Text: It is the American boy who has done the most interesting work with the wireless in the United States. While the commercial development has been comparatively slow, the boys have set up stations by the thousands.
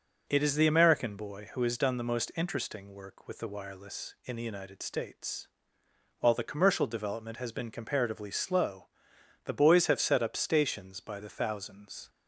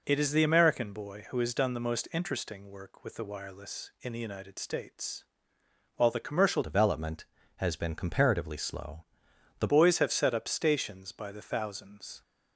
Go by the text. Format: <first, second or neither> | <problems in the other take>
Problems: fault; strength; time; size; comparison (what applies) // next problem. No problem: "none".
first | changes voice from "development" to "the"; from 6.6 to 9.6 s; 3.0 s long